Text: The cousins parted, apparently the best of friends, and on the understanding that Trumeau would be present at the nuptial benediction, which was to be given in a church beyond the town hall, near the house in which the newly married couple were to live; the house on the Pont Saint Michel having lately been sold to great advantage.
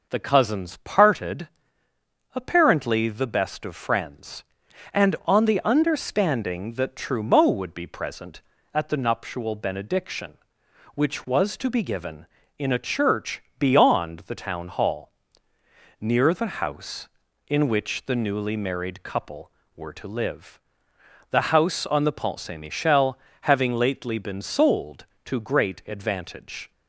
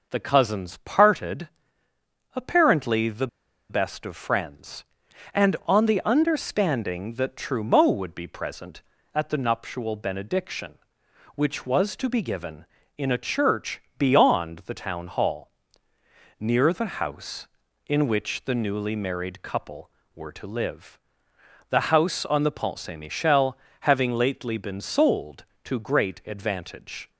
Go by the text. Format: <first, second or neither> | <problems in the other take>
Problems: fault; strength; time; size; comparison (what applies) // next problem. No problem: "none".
first | pauses between "the" and "best"; at 3.2 s; 0.43 s long // pauses between "church" and "beyond"; slight; at 13.8 s; 0.18 s long; slight in the first // pauses between "Michel" and "having"; slight; at 23.5 s; 0.24 s long; slight in the first